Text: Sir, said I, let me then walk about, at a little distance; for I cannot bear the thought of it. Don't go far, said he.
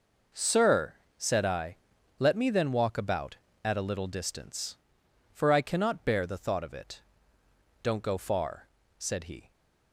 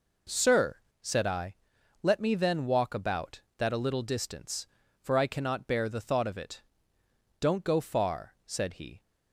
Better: first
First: none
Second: says "that" for "at"; at 3.5 s

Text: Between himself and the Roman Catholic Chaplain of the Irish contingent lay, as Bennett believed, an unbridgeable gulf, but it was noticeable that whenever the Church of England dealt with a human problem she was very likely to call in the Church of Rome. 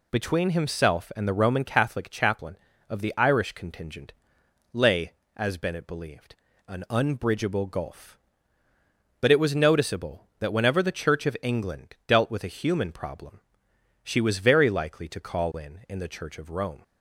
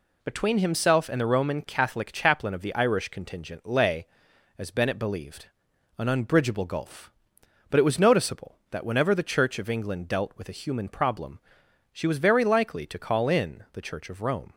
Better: second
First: pauses between "contingent" and "lay"; noticeable; at 4.1 s; 0.62 s long // pauses between "problem" and "she"; noticeable; at 13.3 s; 0.62 s long // says "in" twice; at 15.8 s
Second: pauses between "problem" and "she"; noticeable; at 11.4 s; 0.54 s long

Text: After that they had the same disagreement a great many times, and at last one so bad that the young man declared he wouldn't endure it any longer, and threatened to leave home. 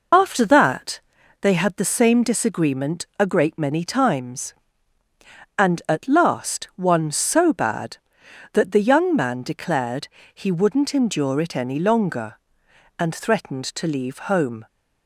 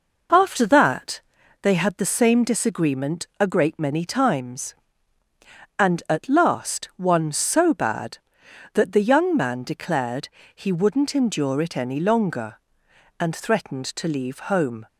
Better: second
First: loses the start of "After"; at 0.1 s; 35 ms // pauses between "that" and "they"; at 0.9 s; 0.42 s long // pauses between "declared" and "he"; slight; at 10.0 s; 0.26 s long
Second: pauses between "that" and "they"; at 1.1 s; 0.42 s long // pauses between "declared" and "he"; slight; at 10.2 s; 0.26 s long

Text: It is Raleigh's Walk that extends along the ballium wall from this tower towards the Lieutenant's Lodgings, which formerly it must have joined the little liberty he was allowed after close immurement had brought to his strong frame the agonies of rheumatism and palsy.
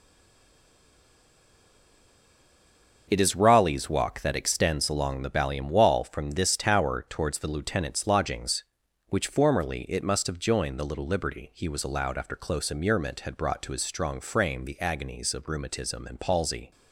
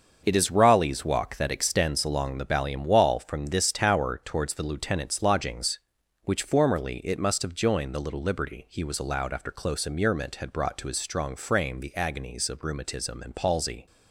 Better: second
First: stays silent before the first word; strong; until 3.0 s; 3.0 s long // starts louder than the rest; until 4.1 s; 6.5 dB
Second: starts louder than the rest; until 1.2 s; 6.5 dB

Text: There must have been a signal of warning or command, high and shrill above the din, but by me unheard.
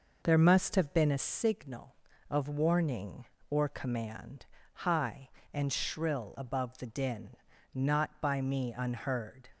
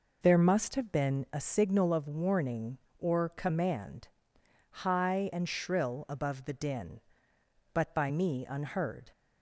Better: second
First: says "not" for "but"; at 7.7 s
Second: none

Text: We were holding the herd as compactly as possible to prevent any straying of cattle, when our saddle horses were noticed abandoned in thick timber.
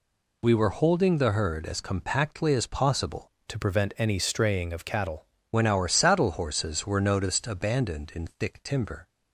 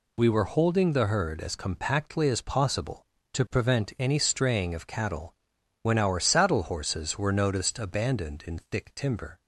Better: second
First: changes voice from "to" to "cattle"; from 3.4 to 5.2 s; 1.8 s long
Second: none

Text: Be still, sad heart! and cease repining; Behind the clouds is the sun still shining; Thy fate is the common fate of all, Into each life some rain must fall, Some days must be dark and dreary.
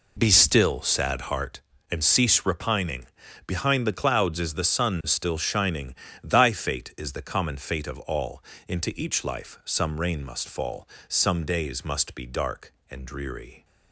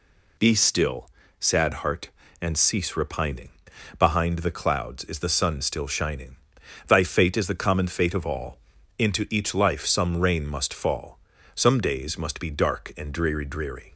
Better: first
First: none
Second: says "dreary" twice; at 13.4 s

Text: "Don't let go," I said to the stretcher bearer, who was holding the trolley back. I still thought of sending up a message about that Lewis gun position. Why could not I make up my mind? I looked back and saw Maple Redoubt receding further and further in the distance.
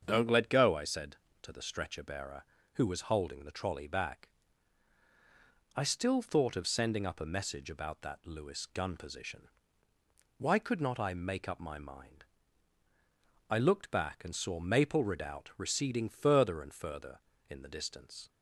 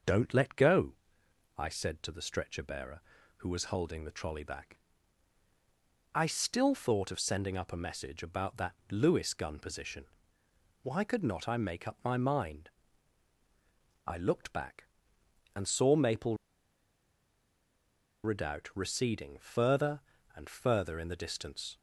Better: first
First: starts louder than the rest; until 1.0 s; 7 dB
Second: starts louder than the rest; noticeable; until 1.7 s; 6 dB // pauses between "Maple" and "Redoubt"; strong; at 16.3 s; 1.8 s long

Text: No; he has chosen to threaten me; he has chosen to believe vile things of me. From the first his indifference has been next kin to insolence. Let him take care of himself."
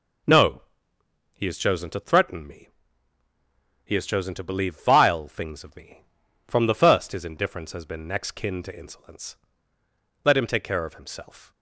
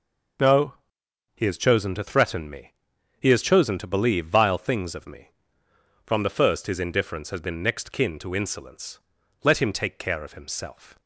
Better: neither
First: none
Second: none

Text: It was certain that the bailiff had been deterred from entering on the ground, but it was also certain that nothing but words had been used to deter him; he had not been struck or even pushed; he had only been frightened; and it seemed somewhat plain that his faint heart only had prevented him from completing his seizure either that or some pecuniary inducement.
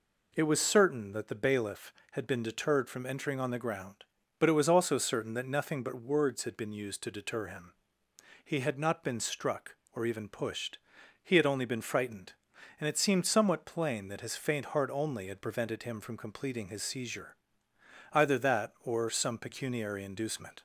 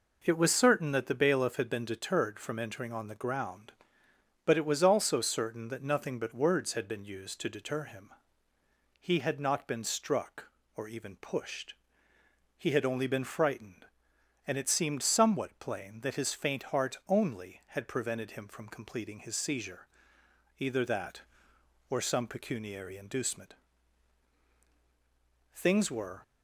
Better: first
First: pauses between "seizure" and "either"; noticeable; at 17.3 s; 0.76 s long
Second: pauses between "seizure" and "either"; noticeable; at 19.8 s; 0.68 s long // goes on to say "Things were"; noticeable; from 25.5 s on; 0.70 s long

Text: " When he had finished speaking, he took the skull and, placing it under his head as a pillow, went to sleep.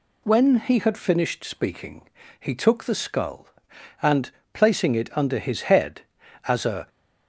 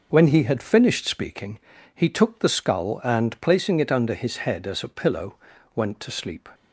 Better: second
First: stops before "pillow went to sleep"; at 6.8 s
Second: none

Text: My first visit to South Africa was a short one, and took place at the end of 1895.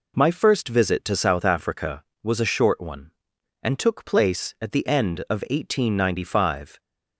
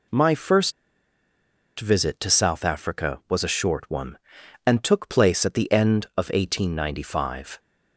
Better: first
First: none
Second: pauses between "first" and "visit"; at 0.7 s; 1.0 s long

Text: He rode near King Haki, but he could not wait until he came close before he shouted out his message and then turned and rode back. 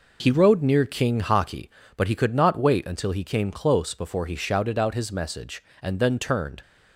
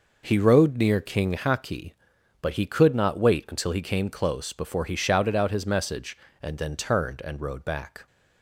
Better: second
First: stops before "and rode back"; at 6.6 s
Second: none

